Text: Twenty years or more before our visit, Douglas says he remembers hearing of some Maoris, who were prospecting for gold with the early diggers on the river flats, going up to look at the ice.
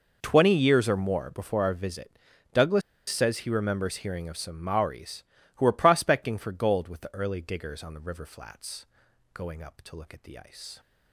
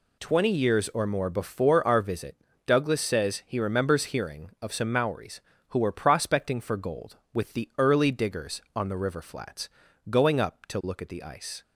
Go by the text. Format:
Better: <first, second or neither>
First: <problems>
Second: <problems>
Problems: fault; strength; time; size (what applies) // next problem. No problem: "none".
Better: second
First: pauses between "Douglas" and "says"; slight; at 2.8 s; 0.28 s long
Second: none